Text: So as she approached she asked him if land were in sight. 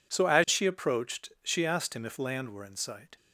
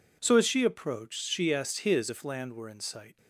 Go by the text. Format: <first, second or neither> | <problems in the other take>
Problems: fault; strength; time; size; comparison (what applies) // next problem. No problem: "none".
first | says "his" for "him"; at 1.8 s